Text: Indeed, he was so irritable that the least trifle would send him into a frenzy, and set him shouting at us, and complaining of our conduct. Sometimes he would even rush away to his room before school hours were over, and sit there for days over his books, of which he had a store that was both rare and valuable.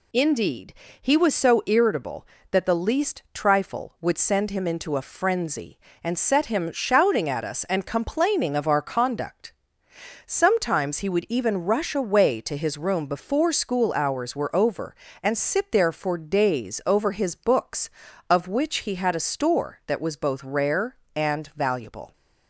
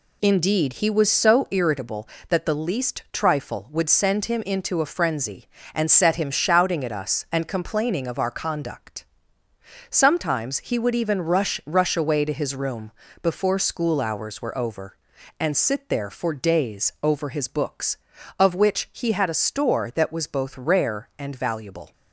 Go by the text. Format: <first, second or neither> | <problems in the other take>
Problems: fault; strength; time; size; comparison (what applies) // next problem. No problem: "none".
first | says "rush" twice; at 11.6 s // pauses between "room" and "before"; slight; at 12.9 s; 0.30 s long